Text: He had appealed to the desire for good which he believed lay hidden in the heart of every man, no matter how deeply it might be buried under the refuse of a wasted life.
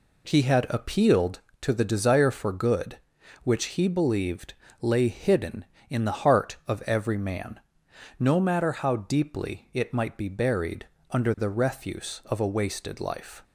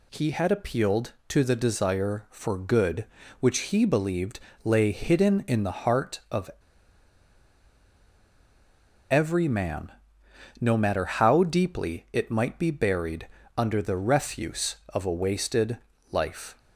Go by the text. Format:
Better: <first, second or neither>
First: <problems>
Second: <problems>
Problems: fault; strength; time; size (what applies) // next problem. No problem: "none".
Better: first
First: pauses between "believed" and "lay"; slight; at 4.5 s; 0.28 s long // pauses between "buried" and "under"; slight; at 10.8 s; 0.24 s long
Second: pauses between "believed" and "lay"; slight; at 4.4 s; 0.24 s long // pauses between "of" and "every"; strong; at 6.5 s; 2.6 s long // pauses between "buried" and "under"; slight; at 13.2 s; 0.28 s long // pauses between "wasted" and "life"; slight; at 15.7 s; 0.32 s long